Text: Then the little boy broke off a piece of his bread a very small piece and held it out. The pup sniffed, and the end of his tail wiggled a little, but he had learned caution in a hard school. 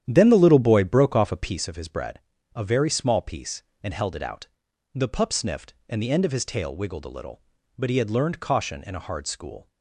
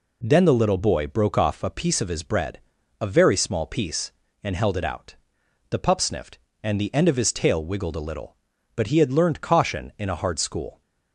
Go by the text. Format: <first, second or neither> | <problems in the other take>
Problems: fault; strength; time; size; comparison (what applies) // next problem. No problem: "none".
second | starts louder than the rest; strong; until 1.6 s; 10 dB // pauses between "bread" and "a"; slight; at 2.1 s; 0.36 s long; also in the second